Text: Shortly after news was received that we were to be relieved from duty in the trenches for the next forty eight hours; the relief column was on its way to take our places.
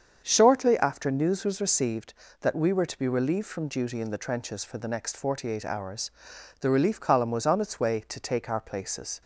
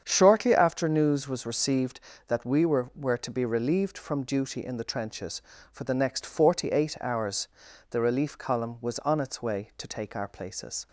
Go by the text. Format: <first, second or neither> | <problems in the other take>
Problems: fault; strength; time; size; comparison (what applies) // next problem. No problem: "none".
first | starts louder than the rest; strong; until 1.0 s; 8 dB; strong in the first // says "were" twice; at 2.9 s